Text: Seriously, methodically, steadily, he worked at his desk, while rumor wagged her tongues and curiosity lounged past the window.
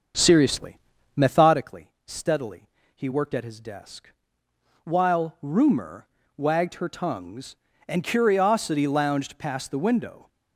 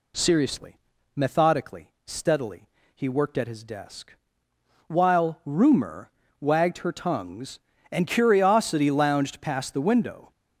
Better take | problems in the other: second | starts louder than the rest; until 1.6 s; 7 dB // pauses between "rumor" and "wagged"; slight; at 6.0 s; 0.30 s long; slight in the second

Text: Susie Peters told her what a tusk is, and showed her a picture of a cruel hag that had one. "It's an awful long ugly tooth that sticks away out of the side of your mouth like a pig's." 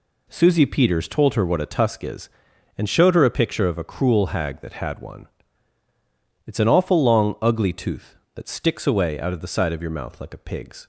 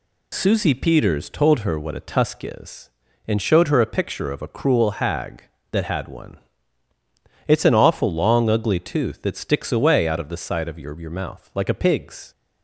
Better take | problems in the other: first | says "your" twice; at 10.9 s

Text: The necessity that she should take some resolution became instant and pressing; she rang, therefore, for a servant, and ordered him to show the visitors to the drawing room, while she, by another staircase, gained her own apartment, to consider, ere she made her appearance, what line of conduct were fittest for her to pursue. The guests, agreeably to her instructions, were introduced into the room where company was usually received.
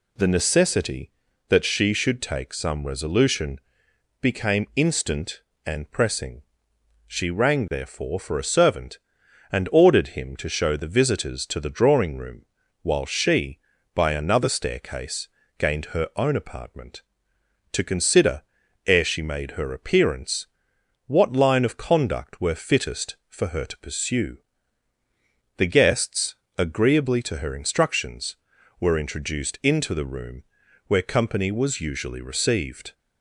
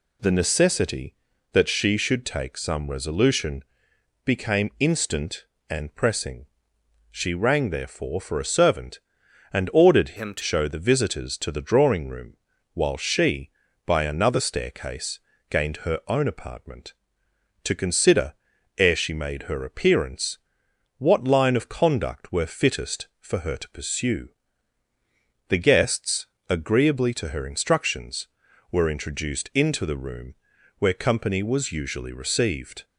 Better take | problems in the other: first | pauses between "resolution" and "became"; noticeable; at 3.6 s; 0.62 s long; noticeable in the first // changes voice from "him" to "to"; from 10.1 to 10.4 s; 0.3 s long // pauses between "room" and "where"; at 30.3 s; 0.44 s long; also in the first

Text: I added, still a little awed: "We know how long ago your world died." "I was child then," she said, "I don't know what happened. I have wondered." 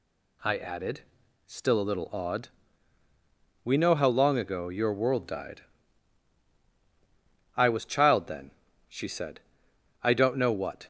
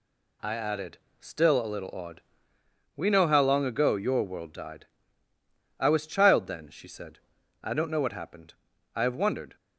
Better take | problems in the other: second | stops before "happened I have wondered"; at 10.8 s

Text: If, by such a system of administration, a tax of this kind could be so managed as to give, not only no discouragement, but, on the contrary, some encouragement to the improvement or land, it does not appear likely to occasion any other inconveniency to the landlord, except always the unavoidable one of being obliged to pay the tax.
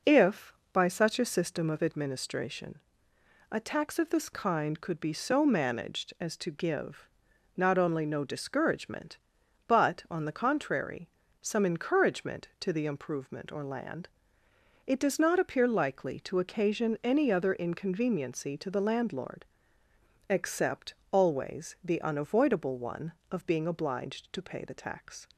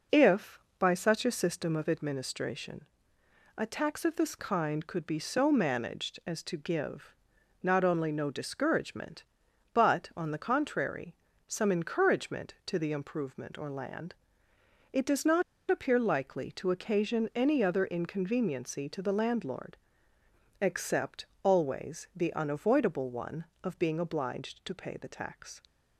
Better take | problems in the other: first | pauses between "not" and "appear"; slight; at 15.4 s; 0.28 s long // pauses between "except" and "always"; slight; at 21.2 s; 0.18 s long; slight in the first

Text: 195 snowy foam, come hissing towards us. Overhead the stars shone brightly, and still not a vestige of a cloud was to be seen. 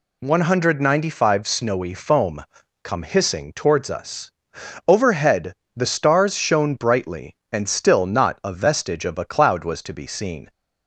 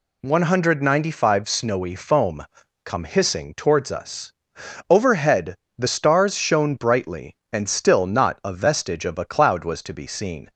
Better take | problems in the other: neither | pauses between "Overhead" and "the"; slight; the same in both

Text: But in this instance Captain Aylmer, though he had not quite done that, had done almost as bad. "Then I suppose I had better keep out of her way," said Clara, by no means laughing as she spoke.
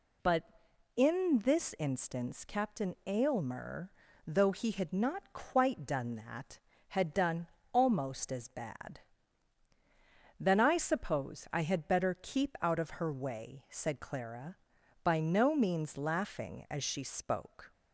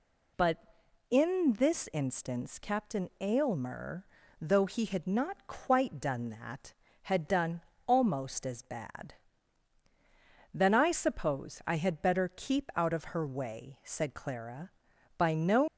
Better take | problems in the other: first | pauses between "done" and "almost"; slight; at 7.5 s; 0.26 s long; slight in the first // stops before "means laughing as she spoke"; at 15.6 s

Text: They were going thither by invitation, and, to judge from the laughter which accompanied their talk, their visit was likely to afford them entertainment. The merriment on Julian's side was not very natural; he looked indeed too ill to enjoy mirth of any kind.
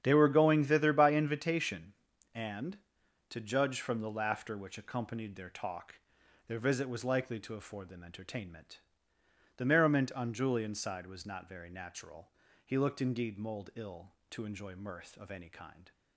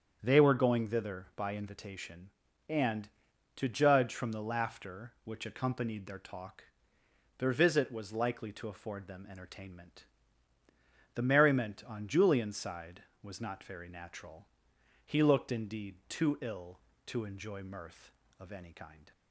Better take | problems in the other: second | starts louder than the rest; strong; until 1.0 s; 9 dB; strong in the second // says "mold" for "too"; at 13.3 s

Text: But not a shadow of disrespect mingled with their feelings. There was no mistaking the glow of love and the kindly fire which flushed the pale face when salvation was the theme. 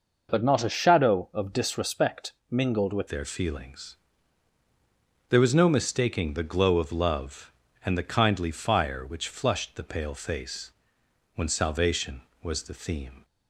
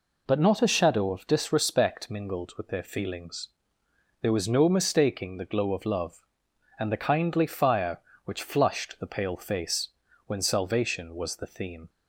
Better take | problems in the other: second | pauses between "disrespect" and "mingled"; slight; at 2.3 s; 0.16 s long // changes voice at "their"; from 3.0 s on; 10.2 s long // pauses between "face" and "when"; noticeable; at 10.7 s; 0.64 s long; also in the second

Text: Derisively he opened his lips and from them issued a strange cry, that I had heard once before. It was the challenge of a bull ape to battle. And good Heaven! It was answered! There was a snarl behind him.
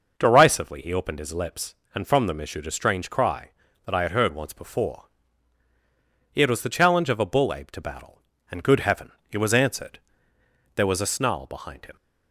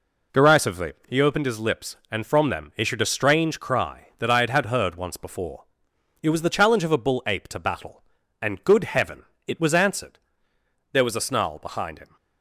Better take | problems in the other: first | pauses between "Derisively" and "he"; slight; at 0.9 s; 0.16 s long // says "had" twice; at 4.4 s

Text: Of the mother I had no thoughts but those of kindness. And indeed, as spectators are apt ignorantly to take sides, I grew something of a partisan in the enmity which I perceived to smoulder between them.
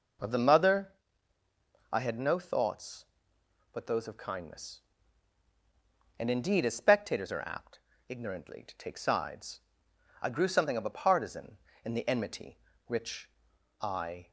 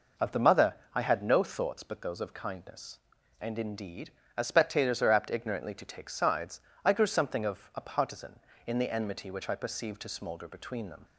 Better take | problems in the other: second | pauses between "mother" and "I"; at 0.9 s; 1.0 s long; slight in the second // pauses between "apt" and "ignorantly"; slight; at 7.7 s; 0.32 s long // pauses between "which" and "I"; noticeable; at 13.3 s; 0.50 s long // stops before "perceived to smoulder between them"; at 14.2 s

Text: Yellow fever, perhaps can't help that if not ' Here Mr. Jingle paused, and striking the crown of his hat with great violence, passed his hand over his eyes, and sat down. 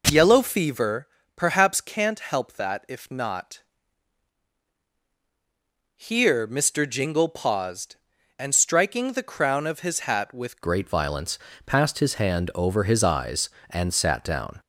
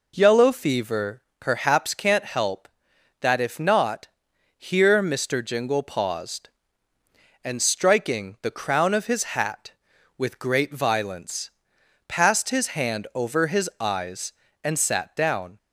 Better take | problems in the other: second | changes voice at "great"; from 10.6 s on; 3.9 s long

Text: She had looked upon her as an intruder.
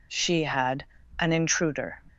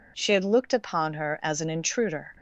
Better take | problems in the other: second | skips "looked upon her as"; at 1.0 s

